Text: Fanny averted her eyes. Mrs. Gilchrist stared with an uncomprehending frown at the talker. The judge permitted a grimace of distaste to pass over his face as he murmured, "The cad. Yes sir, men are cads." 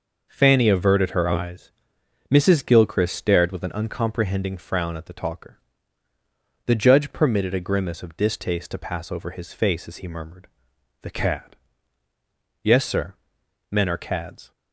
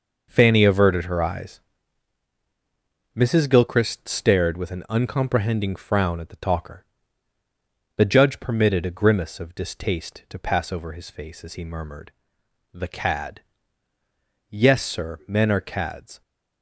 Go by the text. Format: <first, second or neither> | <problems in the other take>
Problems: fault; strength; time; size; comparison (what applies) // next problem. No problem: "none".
neither | none